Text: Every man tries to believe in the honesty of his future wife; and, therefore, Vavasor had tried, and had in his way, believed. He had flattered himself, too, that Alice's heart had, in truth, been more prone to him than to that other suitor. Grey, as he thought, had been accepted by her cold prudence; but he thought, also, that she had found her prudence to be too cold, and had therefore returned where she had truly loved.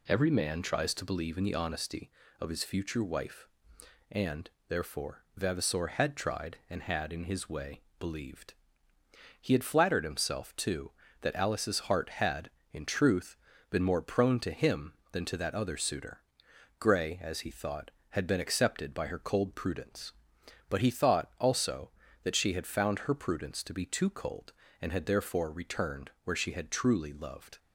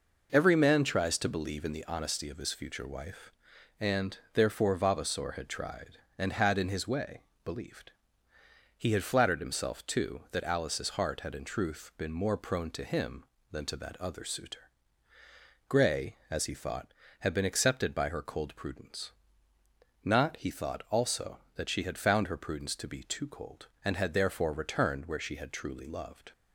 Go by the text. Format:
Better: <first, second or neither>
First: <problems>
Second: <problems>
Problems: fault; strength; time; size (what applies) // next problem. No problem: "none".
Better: first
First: none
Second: says "not" for "but"; at 20.0 s